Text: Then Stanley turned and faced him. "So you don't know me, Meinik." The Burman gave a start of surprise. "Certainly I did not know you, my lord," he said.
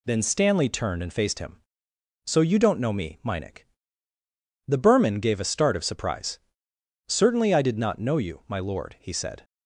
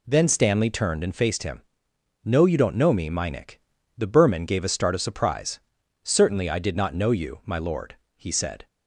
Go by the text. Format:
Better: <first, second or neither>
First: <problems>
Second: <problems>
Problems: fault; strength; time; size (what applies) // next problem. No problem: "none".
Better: first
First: none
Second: says "No" for "So"; at 2.2 s